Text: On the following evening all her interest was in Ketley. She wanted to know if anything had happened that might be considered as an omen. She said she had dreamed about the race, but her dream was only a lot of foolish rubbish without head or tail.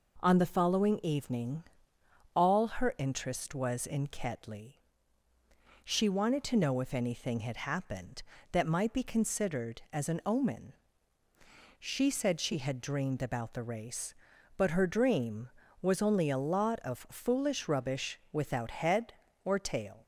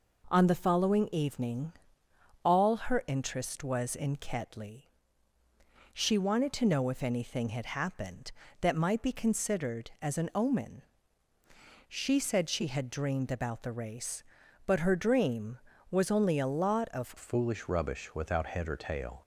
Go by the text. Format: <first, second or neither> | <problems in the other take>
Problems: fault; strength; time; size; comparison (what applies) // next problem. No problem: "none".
first | pauses between "evening" and "all"; noticeable; at 1.7 s; 0.72 s long; noticeable in the first // changes voice at "foolish"; from 17.1 s on; 2.1 s long